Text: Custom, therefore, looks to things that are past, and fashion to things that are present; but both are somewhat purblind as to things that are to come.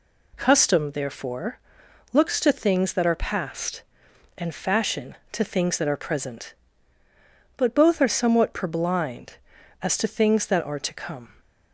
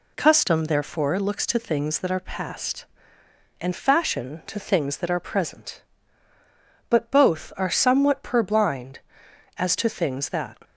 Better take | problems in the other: first | stops before "are to come"; at 10.6 s

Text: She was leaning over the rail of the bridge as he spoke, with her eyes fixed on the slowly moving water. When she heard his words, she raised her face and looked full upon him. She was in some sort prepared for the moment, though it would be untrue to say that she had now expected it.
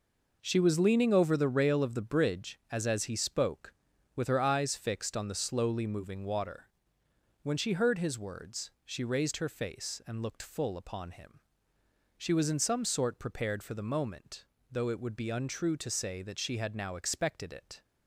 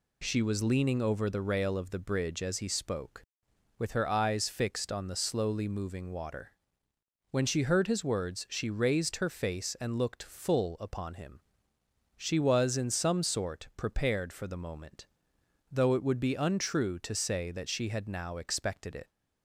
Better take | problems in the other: second | says "as" twice; at 2.8 s

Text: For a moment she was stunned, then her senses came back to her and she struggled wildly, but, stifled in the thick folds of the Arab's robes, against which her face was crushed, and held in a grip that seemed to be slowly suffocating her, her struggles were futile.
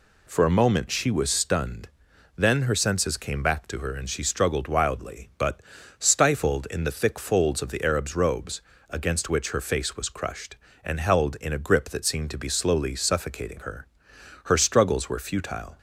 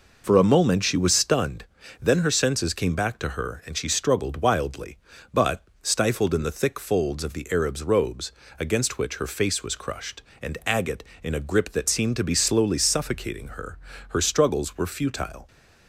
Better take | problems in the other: first | says "agate" for "held"; at 10.6 s

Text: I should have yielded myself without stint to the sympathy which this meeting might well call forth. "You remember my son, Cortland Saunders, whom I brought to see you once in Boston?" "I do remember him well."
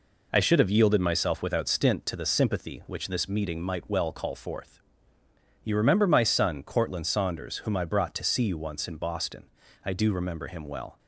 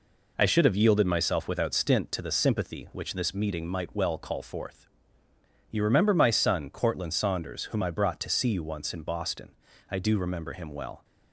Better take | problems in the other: neither | none

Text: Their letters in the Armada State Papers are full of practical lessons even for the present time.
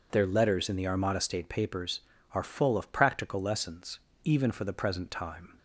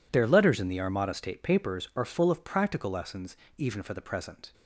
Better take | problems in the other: first | pauses between "lessons" and "even"; slight; at 3.3 s; 0.20 s long; slight in the first // stops before "time"; at 4.5 s

